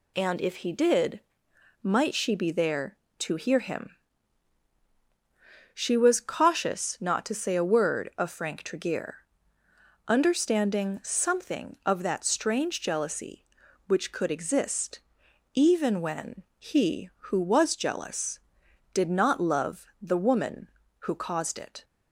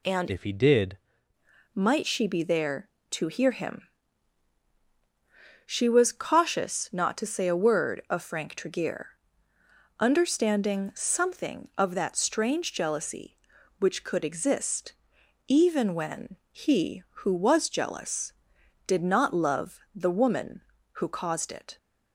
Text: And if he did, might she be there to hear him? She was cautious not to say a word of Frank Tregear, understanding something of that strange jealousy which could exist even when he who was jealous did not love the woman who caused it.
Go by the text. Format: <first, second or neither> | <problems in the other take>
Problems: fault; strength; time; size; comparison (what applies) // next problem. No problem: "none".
first | changes voice from "if" to "did"; from 0.3 to 0.9 s; 0.6 s long // pauses between "exist" and "even"; noticeable; at 14.9 s; 0.54 s long; noticeable in the first // pauses between "love" and "the"; slight; at 19.7 s; 0.16 s long; slight in the first